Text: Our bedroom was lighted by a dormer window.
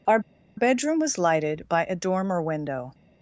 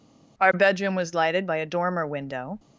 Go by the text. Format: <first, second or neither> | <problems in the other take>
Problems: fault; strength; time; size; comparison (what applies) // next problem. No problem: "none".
second | pauses between "Our" and "bedroom"; at 0.1 s; 0.37 s long